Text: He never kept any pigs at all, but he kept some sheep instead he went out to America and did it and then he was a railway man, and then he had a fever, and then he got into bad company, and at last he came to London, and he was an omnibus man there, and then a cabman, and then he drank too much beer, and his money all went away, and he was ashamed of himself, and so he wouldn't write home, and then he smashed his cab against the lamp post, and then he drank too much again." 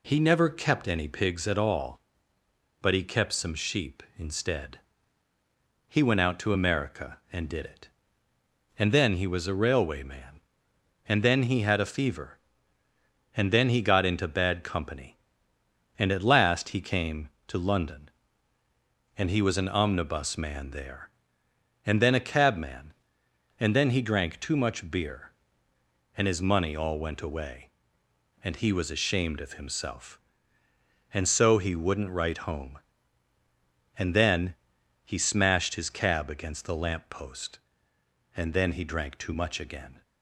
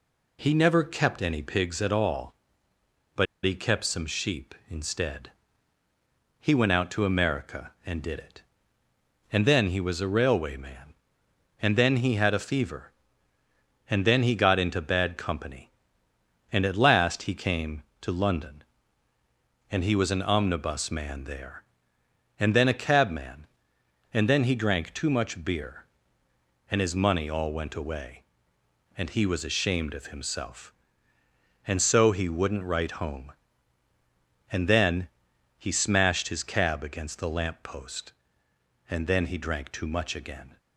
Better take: first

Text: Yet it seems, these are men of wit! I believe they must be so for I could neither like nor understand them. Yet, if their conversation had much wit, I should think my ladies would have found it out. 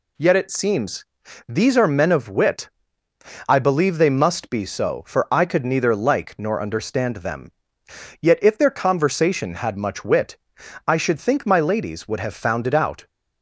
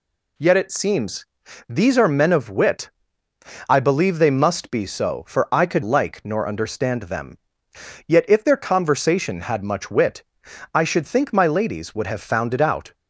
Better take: first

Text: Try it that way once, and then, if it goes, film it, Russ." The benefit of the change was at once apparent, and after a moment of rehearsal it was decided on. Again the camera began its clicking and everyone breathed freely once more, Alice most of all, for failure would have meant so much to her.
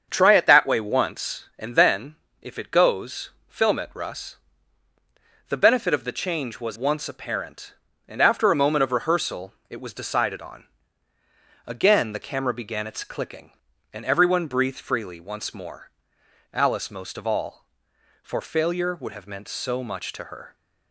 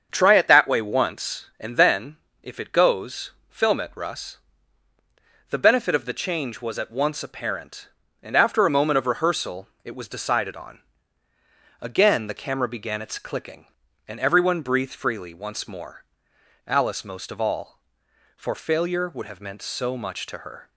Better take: second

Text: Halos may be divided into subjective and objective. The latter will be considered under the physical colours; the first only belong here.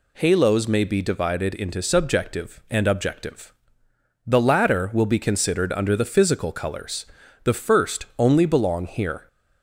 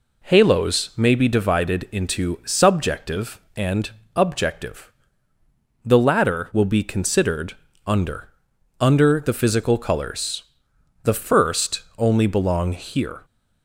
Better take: first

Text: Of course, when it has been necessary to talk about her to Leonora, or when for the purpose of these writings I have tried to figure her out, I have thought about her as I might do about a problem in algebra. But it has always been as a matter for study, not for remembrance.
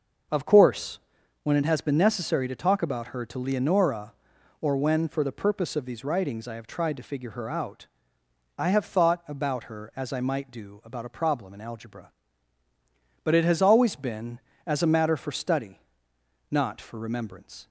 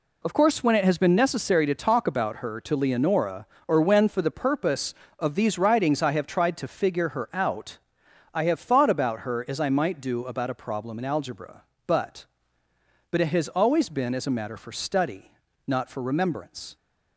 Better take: first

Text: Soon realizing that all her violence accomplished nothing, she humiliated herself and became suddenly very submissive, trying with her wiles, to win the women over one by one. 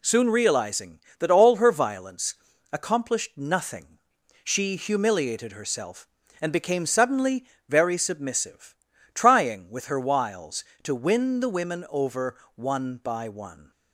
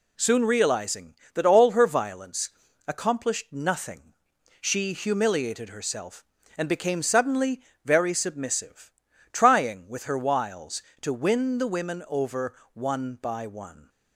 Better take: neither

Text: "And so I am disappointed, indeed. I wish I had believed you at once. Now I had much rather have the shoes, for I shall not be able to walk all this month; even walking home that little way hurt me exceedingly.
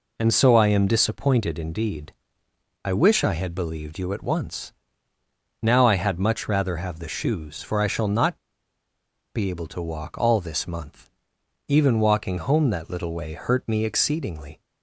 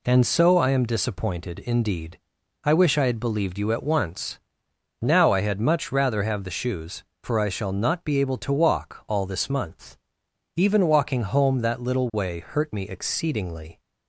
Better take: second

